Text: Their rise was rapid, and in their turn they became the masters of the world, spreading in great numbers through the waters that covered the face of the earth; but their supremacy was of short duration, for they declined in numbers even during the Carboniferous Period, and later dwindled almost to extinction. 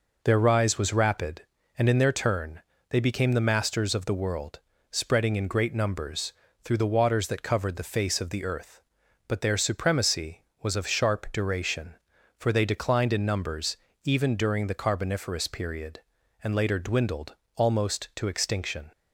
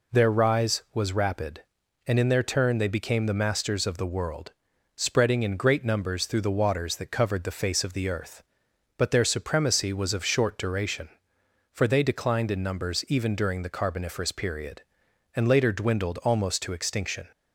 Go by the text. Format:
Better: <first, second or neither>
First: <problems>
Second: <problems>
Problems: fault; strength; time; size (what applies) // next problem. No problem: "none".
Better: second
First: pauses between "turn" and "they"; slight; at 2.6 s; 0.28 s long // pauses between "numbers" and "through"; slight; at 6.3 s; 0.30 s long // says "sharp" for "short"; at 10.8 s // pauses between "numbers" and "even"; slight; at 13.7 s; 0.26 s long // pauses between "dwindled" and "almost"; slight; at 17.3 s; 0.20 s long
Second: none